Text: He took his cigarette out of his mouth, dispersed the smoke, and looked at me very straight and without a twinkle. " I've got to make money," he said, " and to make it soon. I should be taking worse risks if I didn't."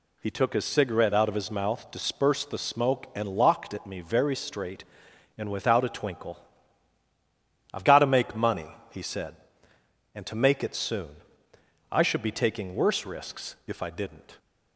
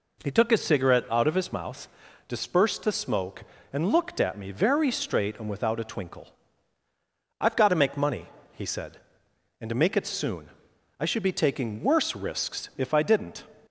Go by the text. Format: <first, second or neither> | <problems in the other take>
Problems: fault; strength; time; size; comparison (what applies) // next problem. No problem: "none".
second | says "locked" for "looked"; at 3.3 s